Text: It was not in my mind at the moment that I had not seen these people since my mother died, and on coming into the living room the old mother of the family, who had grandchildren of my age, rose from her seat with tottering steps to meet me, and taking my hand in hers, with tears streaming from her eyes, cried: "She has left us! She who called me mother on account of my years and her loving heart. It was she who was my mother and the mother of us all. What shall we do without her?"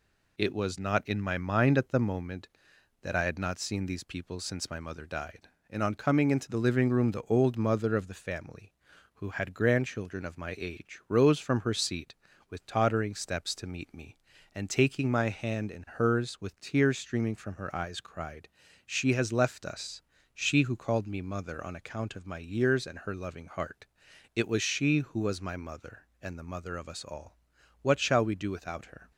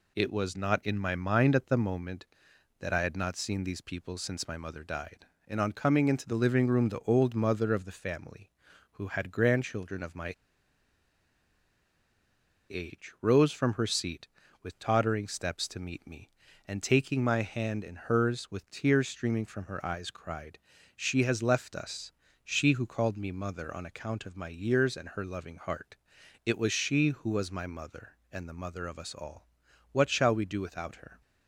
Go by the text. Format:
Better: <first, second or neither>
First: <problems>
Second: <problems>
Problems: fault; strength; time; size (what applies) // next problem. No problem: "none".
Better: first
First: none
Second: pauses between "my" and "age"; strong; at 10.3 s; 2.3 s long